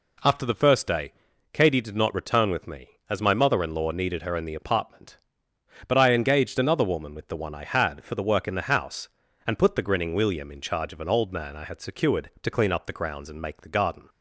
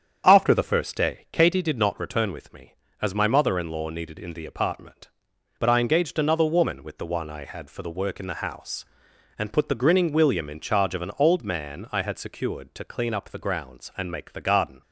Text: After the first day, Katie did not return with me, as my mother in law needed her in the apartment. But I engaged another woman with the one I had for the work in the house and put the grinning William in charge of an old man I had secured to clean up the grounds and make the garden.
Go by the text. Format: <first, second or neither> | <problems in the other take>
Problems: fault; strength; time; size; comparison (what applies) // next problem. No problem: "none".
first | starts louder than the rest; strong; until 1.2 s; 8 dB // skips "her"; at 4.1 s